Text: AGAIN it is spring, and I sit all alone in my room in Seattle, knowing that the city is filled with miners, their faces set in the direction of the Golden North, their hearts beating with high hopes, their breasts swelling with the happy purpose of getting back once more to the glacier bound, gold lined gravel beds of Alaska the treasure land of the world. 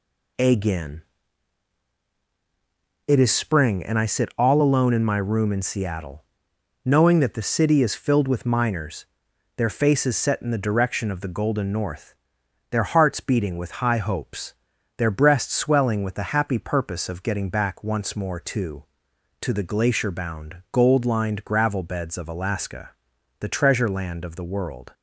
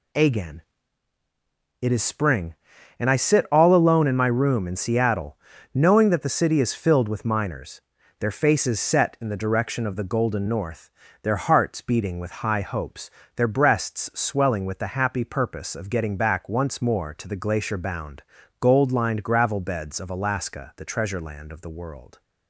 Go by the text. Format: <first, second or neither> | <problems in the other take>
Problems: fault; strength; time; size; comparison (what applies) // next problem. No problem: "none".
second | pauses between "AGAIN" and "it"; strong; at 1.0 s; 2.0 s long; also in the second // says "to" twice; at 19.4 s // pauses between "Alaska" and "the"; noticeable; at 22.9 s; 0.48 s long